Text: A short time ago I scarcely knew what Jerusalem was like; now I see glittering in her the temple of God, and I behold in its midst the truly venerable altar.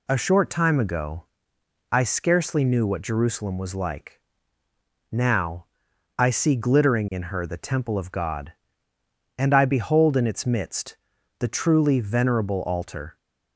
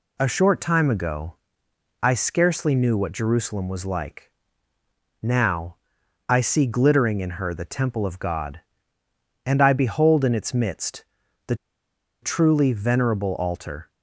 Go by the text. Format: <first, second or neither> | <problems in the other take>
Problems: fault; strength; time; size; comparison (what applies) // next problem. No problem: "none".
first | pauses between "ago" and "I"; noticeable; at 1.3 s; 0.66 s long; noticeable in the first // pauses between "now" and "I"; noticeable; at 5.7 s; 0.52 s long; noticeable in the first // pauses between "midst" and "the"; at 11.0 s; 0.42 s long; also in the first // pauses between "the" and "truly"; noticeable; at 11.5 s; 0.67 s long